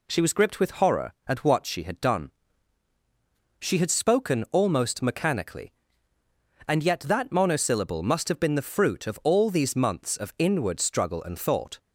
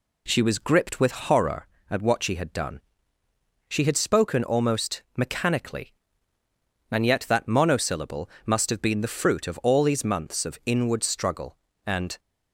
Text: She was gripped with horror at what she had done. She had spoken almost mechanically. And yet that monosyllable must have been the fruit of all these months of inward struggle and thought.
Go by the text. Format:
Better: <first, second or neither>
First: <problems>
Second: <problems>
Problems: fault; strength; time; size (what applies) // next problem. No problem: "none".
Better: first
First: none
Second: pauses between "monosyllable" and "must"; slight; at 8.2 s; 0.16 s long // stops before "thought"; at 12.1 s